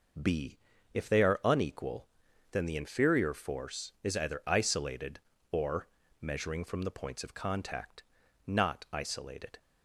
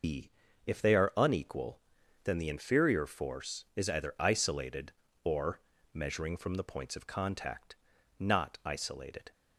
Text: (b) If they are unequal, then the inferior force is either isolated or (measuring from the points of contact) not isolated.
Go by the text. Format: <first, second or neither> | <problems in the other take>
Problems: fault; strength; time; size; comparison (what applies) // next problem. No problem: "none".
first | loses the start of "b"; at 0.0 s; 155 ms